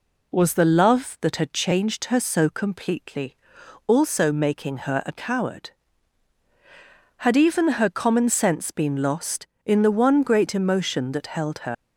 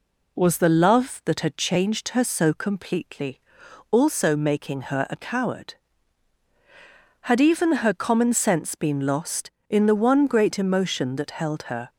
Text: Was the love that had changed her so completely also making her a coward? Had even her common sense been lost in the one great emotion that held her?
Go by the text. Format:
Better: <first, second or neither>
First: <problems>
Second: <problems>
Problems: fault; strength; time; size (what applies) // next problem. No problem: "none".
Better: second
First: pauses between "completely" and "also"; noticeable; at 3.3 s; 0.48 s long // leaves "her" unfinished; at 11.7 s; 100 ms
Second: pauses between "completely" and "also"; noticeable; at 3.4 s; 0.48 s long